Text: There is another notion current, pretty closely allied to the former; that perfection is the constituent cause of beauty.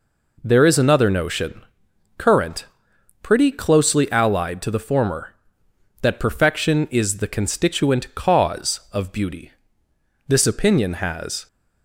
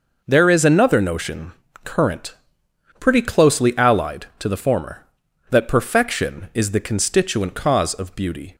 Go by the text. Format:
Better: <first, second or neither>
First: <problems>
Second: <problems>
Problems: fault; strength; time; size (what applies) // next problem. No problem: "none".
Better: second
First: pauses between "notion" and "current"; noticeable; at 1.6 s; 0.56 s long // goes on to say "This opinion has"; noticeable; from 10.2 s on; 1.1 s long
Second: pauses between "notion" and "current"; slight; at 1.5 s; 0.32 s long